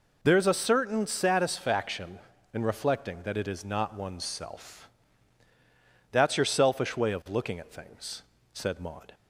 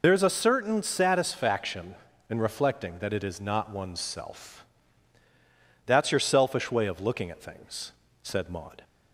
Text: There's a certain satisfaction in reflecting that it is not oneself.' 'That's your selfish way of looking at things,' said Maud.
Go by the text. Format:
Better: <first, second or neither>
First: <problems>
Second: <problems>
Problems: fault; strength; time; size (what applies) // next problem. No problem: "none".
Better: first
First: none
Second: loses the start of "There's"; at 0.0 s; 50 ms